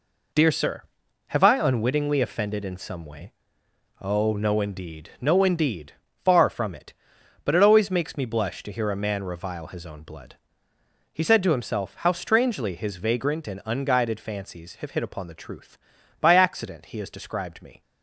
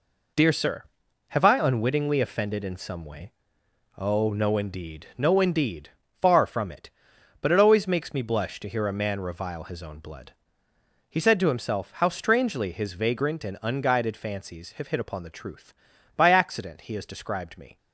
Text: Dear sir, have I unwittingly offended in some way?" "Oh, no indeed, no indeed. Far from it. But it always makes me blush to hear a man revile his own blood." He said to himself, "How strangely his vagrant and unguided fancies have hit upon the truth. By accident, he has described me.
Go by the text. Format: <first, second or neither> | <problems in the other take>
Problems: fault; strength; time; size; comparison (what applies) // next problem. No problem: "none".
neither | none